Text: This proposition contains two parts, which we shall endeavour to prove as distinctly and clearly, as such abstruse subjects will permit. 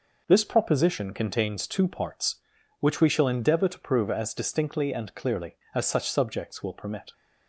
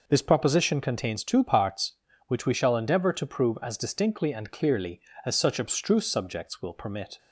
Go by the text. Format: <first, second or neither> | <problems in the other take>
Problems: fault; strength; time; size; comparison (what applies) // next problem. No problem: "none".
second | skips "abstruse"; at 6.0 s